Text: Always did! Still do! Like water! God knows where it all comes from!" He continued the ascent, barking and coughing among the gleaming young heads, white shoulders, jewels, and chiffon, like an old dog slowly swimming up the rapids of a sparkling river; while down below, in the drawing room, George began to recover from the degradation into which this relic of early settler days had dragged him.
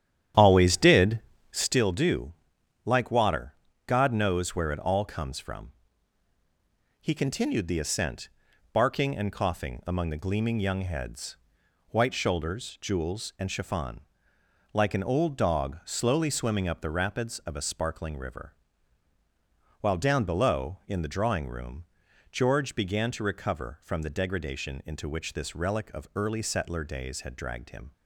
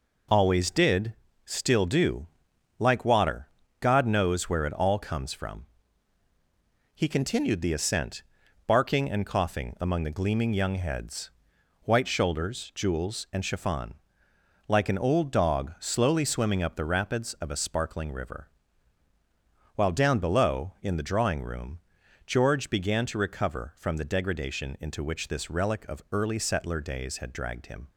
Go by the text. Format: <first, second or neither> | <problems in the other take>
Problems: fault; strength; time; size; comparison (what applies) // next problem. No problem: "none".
second | starts louder than the rest; strong; until 1.8 s; 10.5 dB